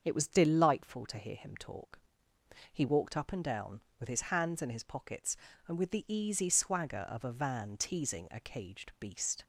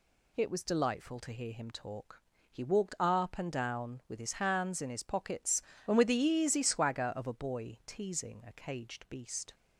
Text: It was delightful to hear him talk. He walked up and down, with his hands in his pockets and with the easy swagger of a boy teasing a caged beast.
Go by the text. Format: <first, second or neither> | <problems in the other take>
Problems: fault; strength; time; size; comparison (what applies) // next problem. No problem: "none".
second | starts louder than the rest; until 1.0 s; 6.5 dB // says "van" for "boy"; at 7.3 s